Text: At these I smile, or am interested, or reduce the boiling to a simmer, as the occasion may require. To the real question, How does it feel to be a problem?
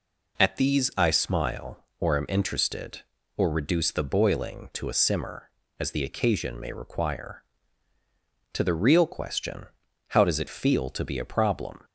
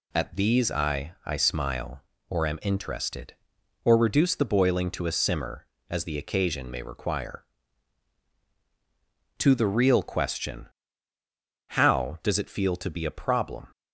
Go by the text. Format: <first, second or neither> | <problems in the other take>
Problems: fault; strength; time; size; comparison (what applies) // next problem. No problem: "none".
first | says "I" twice; at 1.2 s